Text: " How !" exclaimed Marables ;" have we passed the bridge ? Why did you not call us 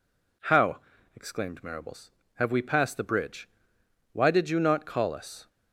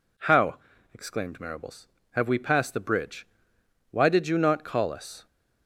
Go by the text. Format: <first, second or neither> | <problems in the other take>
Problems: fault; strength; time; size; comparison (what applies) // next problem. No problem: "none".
neither | none